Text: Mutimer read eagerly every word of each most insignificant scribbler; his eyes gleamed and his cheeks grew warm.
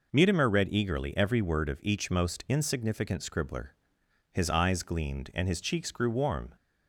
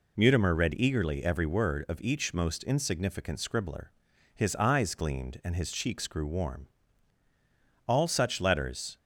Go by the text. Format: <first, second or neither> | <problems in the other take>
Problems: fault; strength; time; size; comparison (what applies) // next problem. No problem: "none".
first | goes on to say "All such letters"; noticeable; from 7.8 s on; 1.1 s long